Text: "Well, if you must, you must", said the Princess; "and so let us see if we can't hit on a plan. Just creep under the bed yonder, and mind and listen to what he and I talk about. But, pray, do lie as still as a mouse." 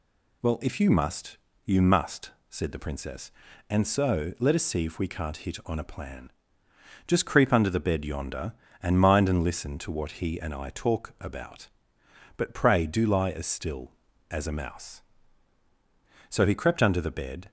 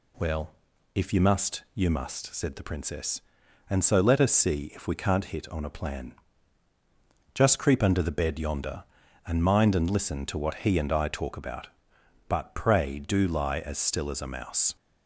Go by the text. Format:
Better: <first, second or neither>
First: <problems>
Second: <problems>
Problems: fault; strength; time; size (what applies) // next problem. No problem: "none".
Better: second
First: goes on to say "So he crept under the bed"; noticeable; from 16.2 s on; 1.2 s long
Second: none